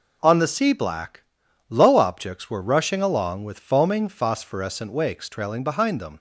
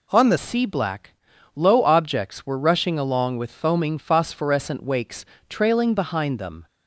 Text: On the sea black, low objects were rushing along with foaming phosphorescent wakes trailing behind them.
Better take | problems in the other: first | changes voice at "sea"; from 0.3 s on; 6.3 s long // pauses between "wakes" and "trailing"; slight; at 5.2 s; 0.24 s long

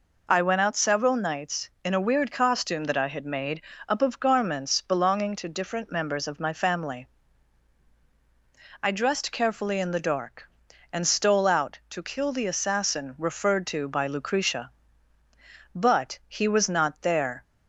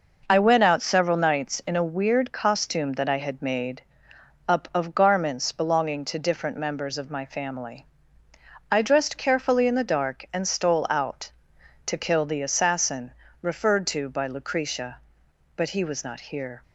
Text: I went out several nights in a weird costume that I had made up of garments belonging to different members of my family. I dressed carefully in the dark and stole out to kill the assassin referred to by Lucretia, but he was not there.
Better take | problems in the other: first | pauses between "made" and "up"; noticeable; at 3.8 s; 0.66 s long; slight in the first // pauses between "assassin" and "referred"; slight; at 13.1 s; 0.30 s long // says "here" for "there"; at 16.1 s

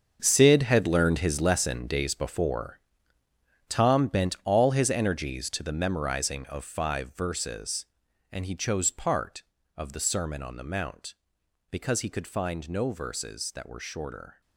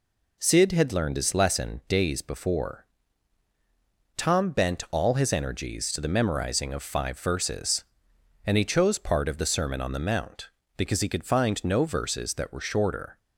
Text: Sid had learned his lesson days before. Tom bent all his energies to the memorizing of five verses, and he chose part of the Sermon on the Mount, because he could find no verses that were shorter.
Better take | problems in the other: second | gets quieter; strong; throughout; 12.5 dB

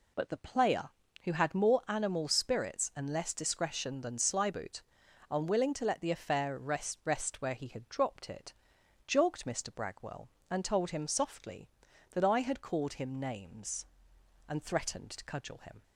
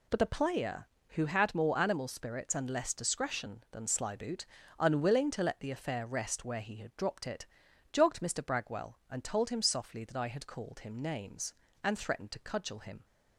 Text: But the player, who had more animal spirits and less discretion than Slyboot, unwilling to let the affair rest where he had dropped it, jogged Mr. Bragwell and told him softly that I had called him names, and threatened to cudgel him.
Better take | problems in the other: second | says "rest" twice; at 7.0 s

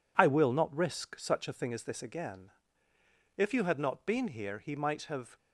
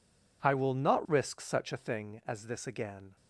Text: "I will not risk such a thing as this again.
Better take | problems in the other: second | goes on to say "If you had not been here he might have"; strong; from 3.3 s on; 2.0 s long

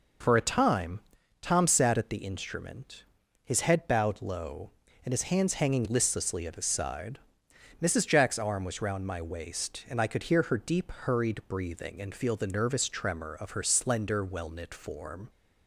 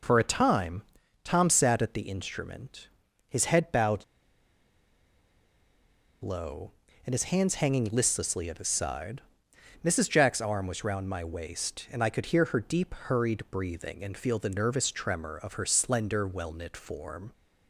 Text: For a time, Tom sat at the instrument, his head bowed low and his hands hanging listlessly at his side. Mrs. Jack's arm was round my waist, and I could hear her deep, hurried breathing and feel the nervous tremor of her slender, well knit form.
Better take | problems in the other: first | pauses between "bowed" and "low"; strong; at 4.0 s; 2.1 s long

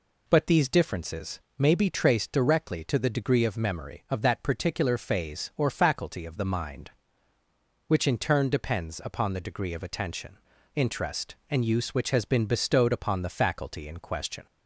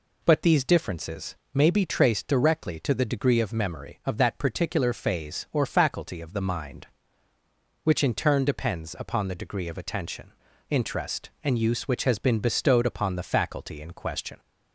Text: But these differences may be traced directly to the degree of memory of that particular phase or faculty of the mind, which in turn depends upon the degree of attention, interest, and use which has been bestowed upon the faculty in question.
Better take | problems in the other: neither | pauses between "differences" and "may"; slight; the same in both

